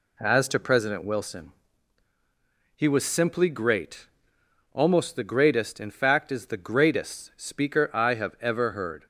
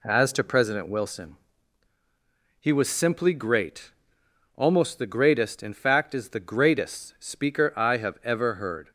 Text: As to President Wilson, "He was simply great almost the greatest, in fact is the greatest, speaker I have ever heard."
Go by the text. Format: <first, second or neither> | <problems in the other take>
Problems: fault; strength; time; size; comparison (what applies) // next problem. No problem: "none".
neither | pauses between "great" and "almost"; noticeable; the same in both